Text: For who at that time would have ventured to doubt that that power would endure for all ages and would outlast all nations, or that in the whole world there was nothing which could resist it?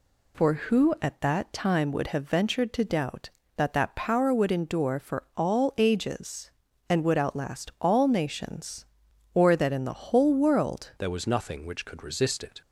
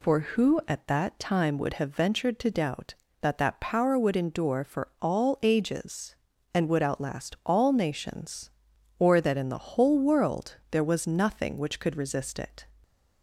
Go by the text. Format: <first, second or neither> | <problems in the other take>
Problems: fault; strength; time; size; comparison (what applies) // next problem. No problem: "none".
second | changes voice at "there"; from 10.9 s on; 1.7 s long